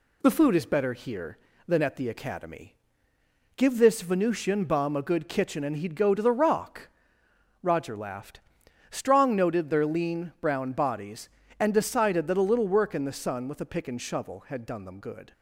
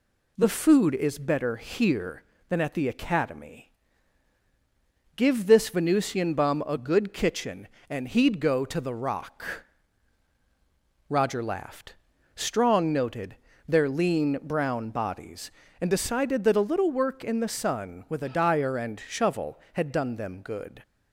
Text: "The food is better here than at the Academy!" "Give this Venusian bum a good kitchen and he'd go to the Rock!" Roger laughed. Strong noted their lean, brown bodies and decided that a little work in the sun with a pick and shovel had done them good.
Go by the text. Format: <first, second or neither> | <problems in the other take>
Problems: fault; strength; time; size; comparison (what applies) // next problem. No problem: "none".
first | pauses between "noted" and "their"; slight; at 13.3 s; 0.32 s long // says "dyer" for "pick"; at 18.2 s